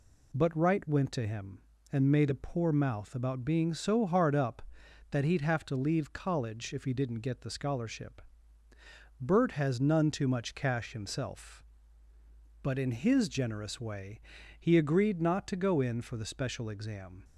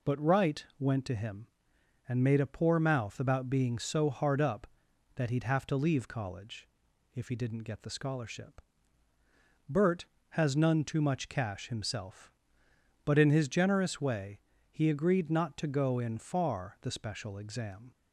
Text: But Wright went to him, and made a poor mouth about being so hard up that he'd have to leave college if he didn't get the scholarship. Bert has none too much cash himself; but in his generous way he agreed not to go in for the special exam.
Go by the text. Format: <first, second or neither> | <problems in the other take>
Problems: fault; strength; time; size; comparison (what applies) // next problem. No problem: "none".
first | pauses between "college" and "if"; noticeable; at 6.6 s; 0.48 s long // pauses between "way" and "he"; slight; at 14.3 s; 0.32 s long; also in the first // says "far" for "for"; at 16.1 s